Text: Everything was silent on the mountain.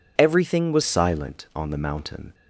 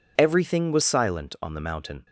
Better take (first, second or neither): second